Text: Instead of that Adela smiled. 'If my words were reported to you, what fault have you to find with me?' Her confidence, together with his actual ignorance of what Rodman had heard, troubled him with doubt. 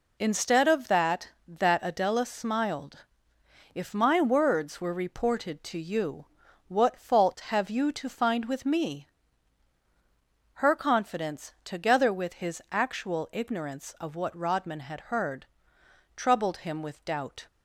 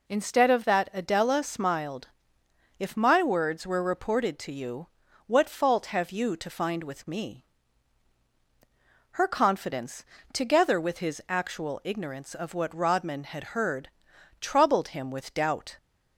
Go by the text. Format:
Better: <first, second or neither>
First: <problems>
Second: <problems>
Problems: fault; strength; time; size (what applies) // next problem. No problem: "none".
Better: second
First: says "that" twice; at 1.4 s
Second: none